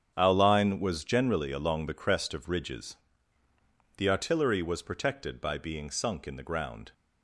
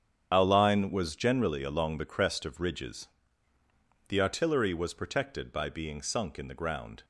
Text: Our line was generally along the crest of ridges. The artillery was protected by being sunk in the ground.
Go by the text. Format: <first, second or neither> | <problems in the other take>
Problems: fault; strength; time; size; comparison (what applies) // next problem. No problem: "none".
first | loses the start of "Our"; at 0.3 s; 55 ms // starts louder than the rest; strong; until 1.3 s; 8 dB; strong in the first